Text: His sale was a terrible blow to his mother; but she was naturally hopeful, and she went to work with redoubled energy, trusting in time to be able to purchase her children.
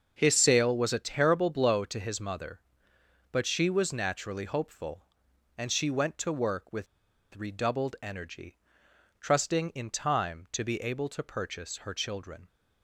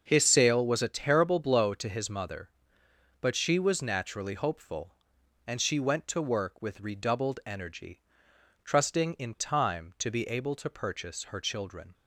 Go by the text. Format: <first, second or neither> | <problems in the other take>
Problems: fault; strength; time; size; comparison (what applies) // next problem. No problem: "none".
second | starts louder than the rest; until 1.1 s; 6.5 dB; also in the second // pauses between "with" and "redoubled"; noticeable; at 6.8 s; 0.48 s long